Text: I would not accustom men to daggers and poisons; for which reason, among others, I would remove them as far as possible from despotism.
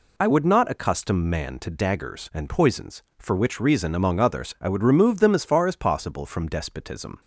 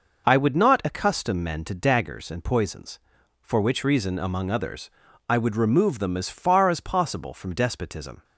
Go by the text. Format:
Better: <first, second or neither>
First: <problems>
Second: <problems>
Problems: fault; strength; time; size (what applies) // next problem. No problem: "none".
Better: second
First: says "man" for "men"; at 1.2 s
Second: none